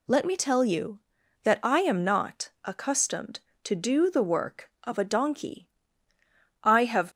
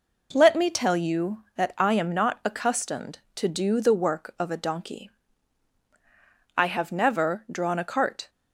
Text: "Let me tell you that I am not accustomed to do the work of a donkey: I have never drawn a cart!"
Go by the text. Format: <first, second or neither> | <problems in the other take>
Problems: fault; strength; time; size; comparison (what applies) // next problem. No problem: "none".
second | stops before "never drawn a cart"; at 7.1 s